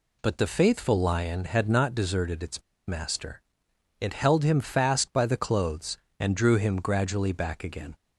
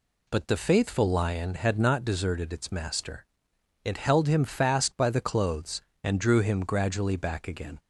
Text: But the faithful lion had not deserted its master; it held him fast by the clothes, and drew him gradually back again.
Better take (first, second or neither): second